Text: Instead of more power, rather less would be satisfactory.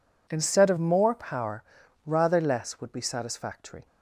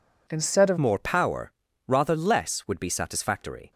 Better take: first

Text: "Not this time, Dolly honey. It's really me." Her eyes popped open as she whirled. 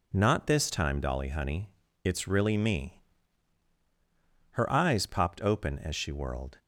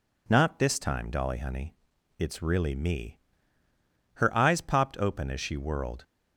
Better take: neither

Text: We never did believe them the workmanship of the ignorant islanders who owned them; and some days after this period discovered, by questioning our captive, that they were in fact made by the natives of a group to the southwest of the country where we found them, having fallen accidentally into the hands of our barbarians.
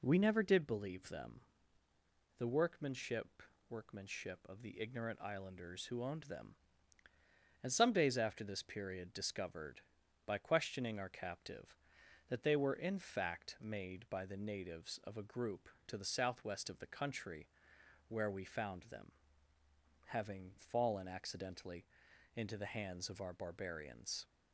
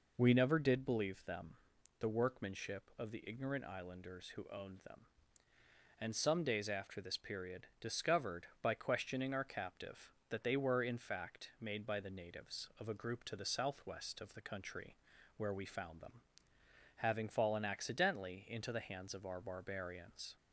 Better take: second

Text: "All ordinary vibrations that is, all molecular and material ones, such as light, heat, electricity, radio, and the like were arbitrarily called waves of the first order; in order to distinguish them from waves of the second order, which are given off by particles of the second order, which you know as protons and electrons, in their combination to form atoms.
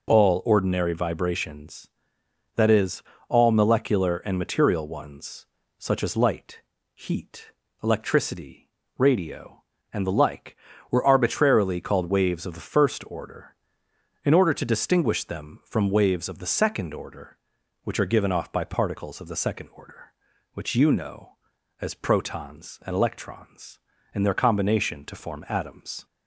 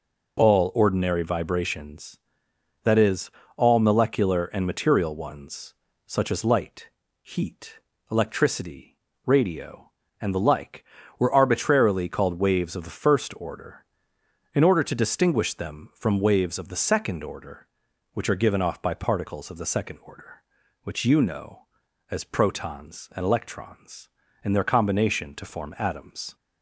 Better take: neither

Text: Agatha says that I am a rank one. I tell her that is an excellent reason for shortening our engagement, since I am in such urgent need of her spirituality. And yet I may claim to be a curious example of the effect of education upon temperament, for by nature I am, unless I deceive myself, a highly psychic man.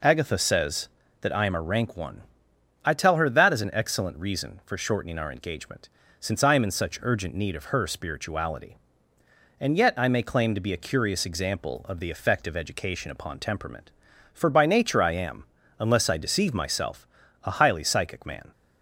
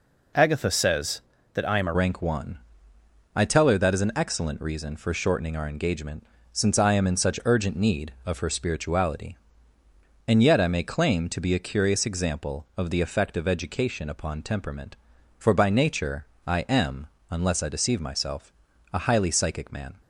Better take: first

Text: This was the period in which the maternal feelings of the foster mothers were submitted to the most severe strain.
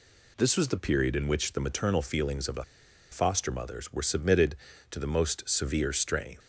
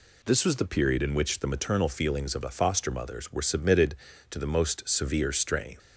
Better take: second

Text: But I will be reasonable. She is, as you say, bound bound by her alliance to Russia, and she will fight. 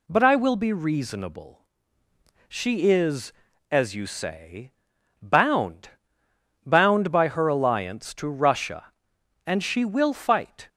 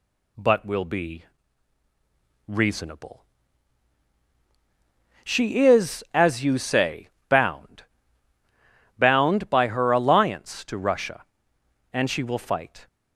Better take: first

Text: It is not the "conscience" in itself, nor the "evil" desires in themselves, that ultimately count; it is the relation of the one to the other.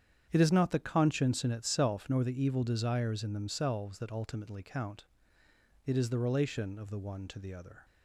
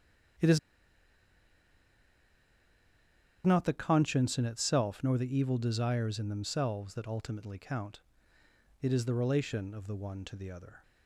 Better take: first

